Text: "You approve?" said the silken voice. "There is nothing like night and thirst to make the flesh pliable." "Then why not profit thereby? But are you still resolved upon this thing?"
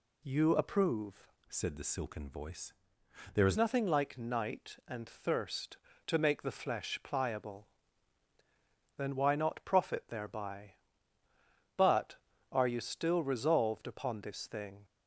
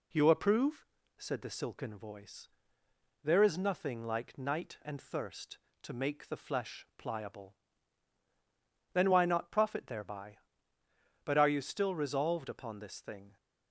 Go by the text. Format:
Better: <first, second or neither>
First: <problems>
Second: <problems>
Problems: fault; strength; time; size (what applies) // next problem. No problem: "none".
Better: second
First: changes voice from "said" to "is"; from 1.4 to 3.5 s; 2.1 s long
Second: none